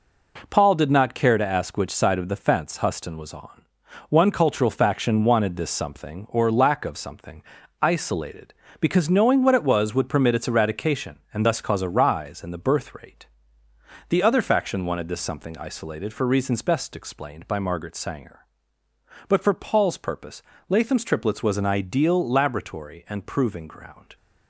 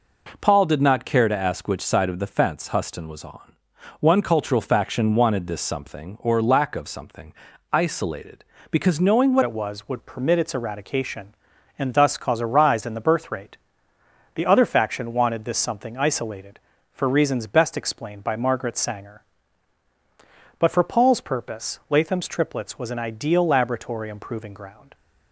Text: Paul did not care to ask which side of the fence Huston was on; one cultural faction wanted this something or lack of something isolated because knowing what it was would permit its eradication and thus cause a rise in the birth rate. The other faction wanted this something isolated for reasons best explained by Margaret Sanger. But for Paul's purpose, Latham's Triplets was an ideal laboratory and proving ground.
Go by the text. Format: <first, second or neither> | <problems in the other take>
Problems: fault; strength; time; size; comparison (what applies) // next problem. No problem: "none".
first | pauses between "something" and "isolated"; at 7.3 s; 0.38 s long; also in the first // changes voice at "it"; from 9.4 s on; 15.5 s long